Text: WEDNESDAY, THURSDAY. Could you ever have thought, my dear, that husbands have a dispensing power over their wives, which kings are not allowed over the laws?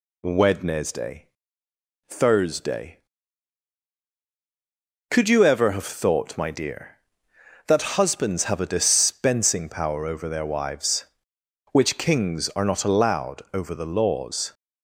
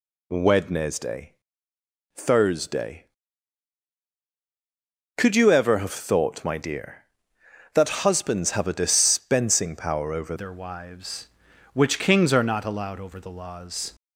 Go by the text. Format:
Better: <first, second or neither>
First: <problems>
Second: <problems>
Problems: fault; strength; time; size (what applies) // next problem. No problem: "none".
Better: first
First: none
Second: changes voice at "their"; from 10.3 s on; 3.6 s long